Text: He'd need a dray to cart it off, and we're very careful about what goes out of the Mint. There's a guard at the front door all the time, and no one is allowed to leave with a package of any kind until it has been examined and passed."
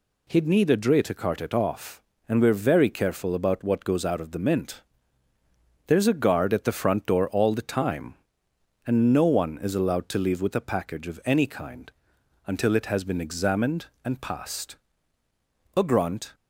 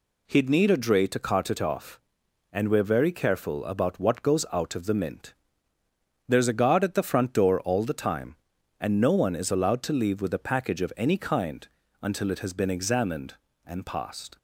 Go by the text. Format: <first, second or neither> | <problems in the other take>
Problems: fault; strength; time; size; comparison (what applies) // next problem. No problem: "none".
second | pauses between "kind" and "until"; noticeable; at 11.9 s; 0.56 s long; slight in the second // goes on to say "A grunt"; from 15.7 s on; 0.56 s long